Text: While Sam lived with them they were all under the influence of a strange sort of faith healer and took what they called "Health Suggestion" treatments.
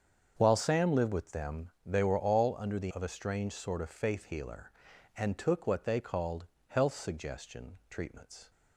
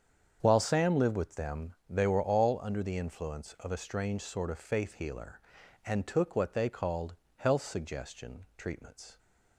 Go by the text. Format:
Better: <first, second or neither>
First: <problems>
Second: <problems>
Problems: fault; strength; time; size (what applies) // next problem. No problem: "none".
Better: second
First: starts louder than the rest; strong; until 1.3 s; 7 dB // skips "influence"; at 2.9 s // pauses between "called" and "Health"; slight; at 6.4 s; 0.24 s long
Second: starts louder than the rest; strong; until 1.4 s; 7.5 dB // pauses between "called" and "Health"; slight; at 7.1 s; 0.24 s long